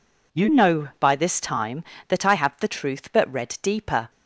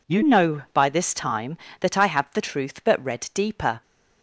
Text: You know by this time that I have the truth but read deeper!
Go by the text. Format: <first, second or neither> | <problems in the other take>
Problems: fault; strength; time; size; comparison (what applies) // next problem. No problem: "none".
neither | none